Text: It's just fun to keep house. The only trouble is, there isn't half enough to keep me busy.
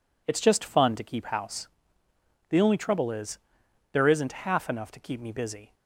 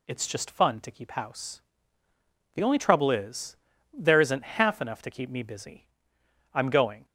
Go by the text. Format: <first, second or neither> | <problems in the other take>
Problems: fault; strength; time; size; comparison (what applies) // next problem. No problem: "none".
first | goes on to say "I'm going"; from 6.5 s on; 0.52 s long